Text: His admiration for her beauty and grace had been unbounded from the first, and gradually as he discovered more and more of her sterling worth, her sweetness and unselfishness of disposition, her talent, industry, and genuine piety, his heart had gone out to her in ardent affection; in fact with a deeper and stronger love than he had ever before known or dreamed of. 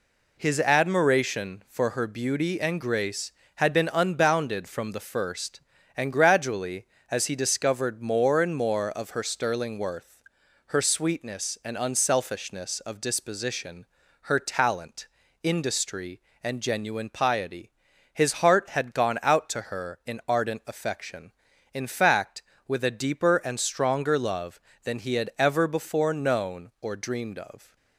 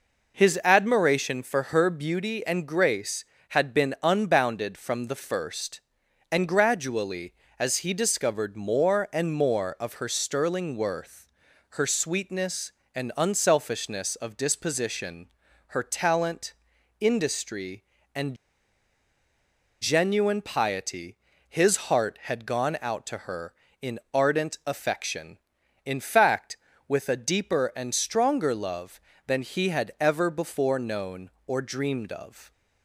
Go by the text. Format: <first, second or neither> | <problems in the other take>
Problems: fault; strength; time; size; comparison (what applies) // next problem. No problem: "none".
first | pauses between "and" and "genuine"; strong; at 18.3 s; 1.4 s long